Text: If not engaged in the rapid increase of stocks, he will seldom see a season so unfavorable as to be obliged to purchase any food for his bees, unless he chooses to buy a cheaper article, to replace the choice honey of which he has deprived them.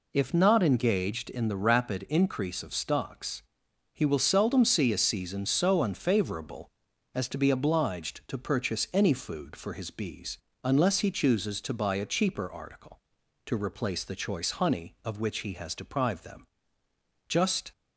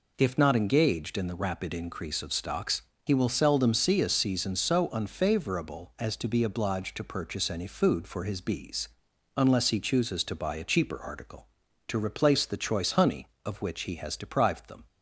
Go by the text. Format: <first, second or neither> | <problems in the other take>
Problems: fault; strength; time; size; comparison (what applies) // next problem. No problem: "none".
second | goes on to say "Just"; slight; from 17.2 s on; 0.44 s long